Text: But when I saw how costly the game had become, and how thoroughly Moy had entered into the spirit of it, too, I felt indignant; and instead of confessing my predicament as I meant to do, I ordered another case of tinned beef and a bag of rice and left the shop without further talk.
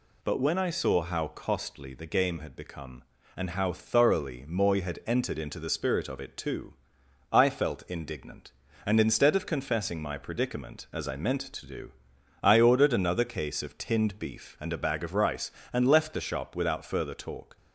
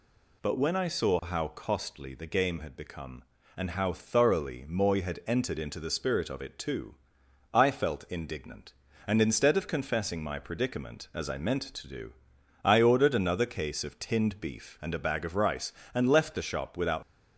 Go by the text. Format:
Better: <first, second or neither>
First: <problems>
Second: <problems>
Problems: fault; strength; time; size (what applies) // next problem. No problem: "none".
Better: first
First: none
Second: stops before "further talk"; at 17.0 s